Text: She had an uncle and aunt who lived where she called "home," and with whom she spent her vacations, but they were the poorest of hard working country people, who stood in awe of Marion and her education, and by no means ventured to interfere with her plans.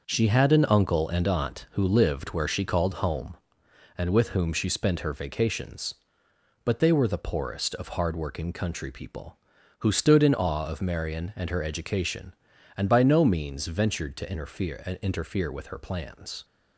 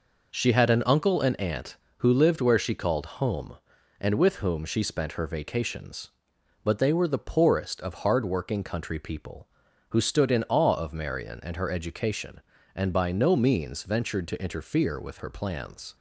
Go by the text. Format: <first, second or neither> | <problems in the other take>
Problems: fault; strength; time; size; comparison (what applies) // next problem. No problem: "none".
second | starts louder than the rest; noticeable; until 1.0 s; 6 dB // says "interfere" twice; at 15.0 s